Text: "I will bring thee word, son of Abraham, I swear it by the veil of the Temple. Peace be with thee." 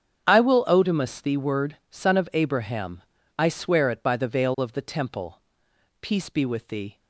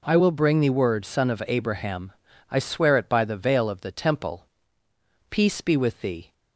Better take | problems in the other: second | starts louder than the rest; strong; until 1.3 s; 8.5 dB // says "odemus" for "bring"; at 0.6 s

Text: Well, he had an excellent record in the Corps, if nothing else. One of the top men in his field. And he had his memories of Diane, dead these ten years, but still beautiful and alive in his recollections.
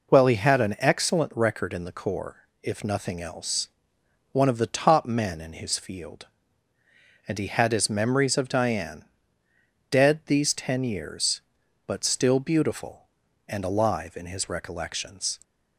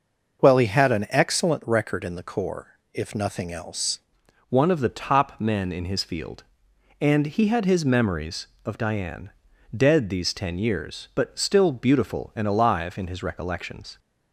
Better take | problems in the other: first | changes voice at "One"; from 4.4 s on; 9.5 s long

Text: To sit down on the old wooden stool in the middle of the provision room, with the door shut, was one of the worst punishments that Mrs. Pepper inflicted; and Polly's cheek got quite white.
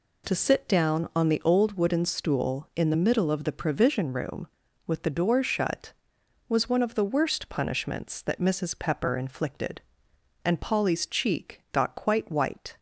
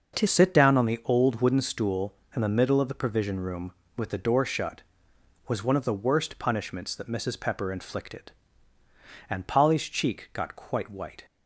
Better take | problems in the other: first | starts louder than the rest; until 1.2 s; 6 dB // changes voice at "sit"; from 0.2 s on; 11.0 s long

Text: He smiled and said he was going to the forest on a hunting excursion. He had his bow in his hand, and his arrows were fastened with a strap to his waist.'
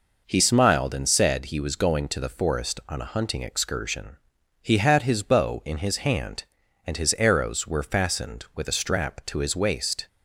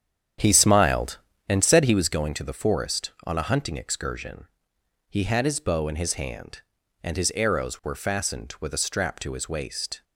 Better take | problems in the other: first | starts louder than the rest; strong; until 2.2 s; 9 dB

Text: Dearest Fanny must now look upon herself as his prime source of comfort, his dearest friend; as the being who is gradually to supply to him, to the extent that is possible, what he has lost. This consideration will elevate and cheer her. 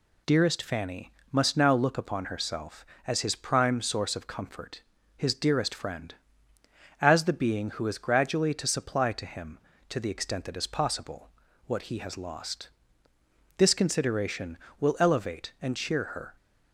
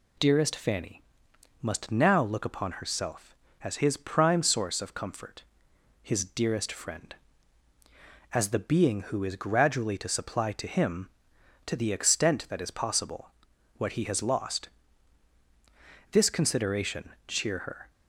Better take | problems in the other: first | pauses between "Fanny" and "must"; noticeable; at 1.0 s; 0.62 s long; slight in the first // skips "will elevate and"; at 17.1 s

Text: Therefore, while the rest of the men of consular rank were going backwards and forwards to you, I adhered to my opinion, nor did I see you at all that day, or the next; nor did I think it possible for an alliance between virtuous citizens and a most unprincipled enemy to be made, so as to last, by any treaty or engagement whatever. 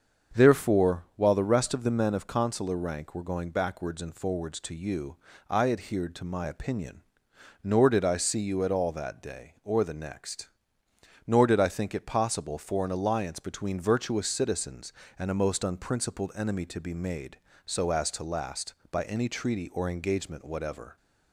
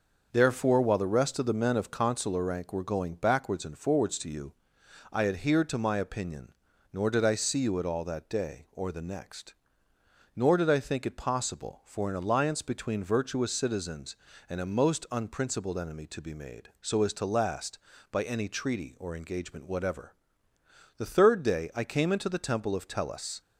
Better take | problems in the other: first | starts louder than the rest; until 1.3 s; 6 dB; also in the first // goes on to say "The third day I came into the temple of Tellus"; strong; from 20.9 s on; 2.4 s long

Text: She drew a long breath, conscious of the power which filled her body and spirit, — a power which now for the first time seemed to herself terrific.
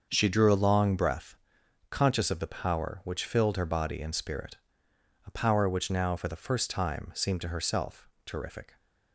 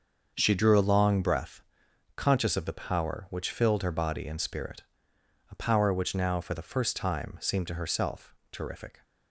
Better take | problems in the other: neither | starts louder than the rest; the same in both // pauses between "herself" and "terrific"; slight; the same in both

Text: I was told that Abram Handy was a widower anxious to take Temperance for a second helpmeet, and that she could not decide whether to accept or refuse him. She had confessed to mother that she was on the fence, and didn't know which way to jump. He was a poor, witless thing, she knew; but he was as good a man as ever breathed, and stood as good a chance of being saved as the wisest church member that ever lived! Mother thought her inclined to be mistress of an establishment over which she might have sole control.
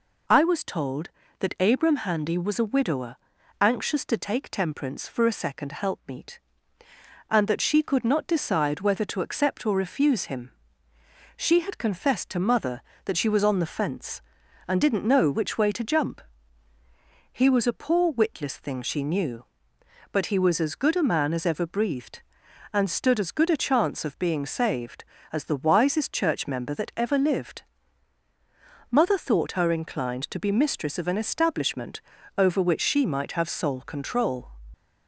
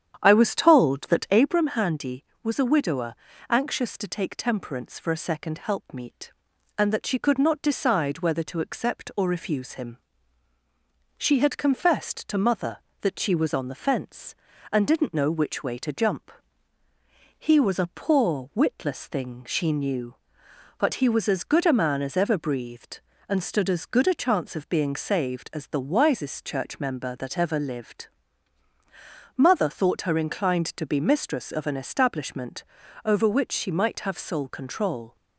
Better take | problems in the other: first | starts louder than the rest; strong; until 1.6 s; 9 dB // pauses between "widower" and "anxious"; slight; at 3.1 s; 0.34 s long; also in the first // pauses between "establishment" and "over"; at 32.6 s; 0.40 s long; also in the first

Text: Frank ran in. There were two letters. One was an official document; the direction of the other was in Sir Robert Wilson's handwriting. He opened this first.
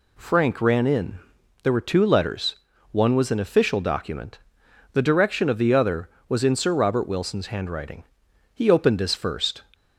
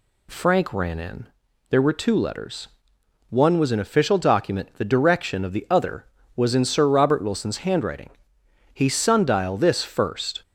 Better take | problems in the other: first | says "sundial" for "opened"; at 8.8 s

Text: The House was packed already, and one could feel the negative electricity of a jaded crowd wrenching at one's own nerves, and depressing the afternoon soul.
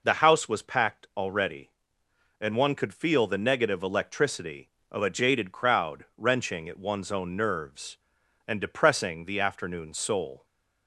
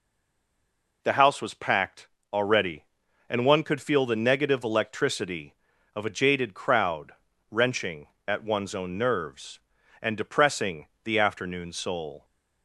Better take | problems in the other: first | stays silent before the first word; until 1.0 s; 1.0 s long // pauses between "packed" and "already"; slight; at 2.0 s; 0.22 s long // pauses between "crowd" and "wrenching"; at 7.1 s; 0.38 s long // pauses between "depressing" and "the"; slight; at 10.8 s; 0.18 s long

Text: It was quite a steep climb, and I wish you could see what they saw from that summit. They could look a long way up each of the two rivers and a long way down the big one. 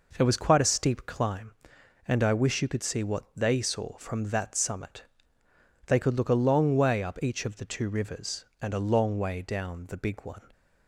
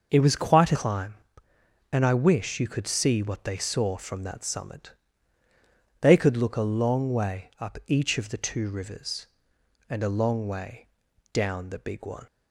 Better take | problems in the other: first | starts louder than the rest; noticeable; until 1.1 s; 6 dB // skips "steep"; at 0.7 s // pauses between "way" and "down"; noticeable; at 10.8 s; 0.46 s long

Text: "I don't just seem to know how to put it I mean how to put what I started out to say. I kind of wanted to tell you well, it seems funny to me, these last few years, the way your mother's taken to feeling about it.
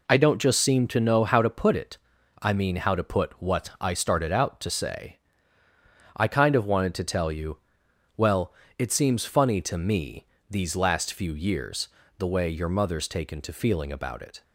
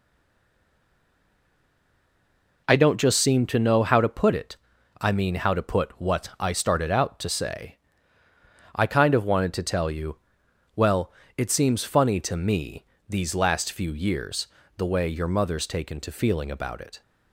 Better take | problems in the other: first | stays silent before the first word; strong; until 2.6 s; 2.6 s long // pauses between "it" and "I"; noticeable; at 4.5 s; 0.46 s long; noticeable in the first // pauses between "you" and "well"; noticeable; at 10.1 s; 0.62 s long; noticeable in the first

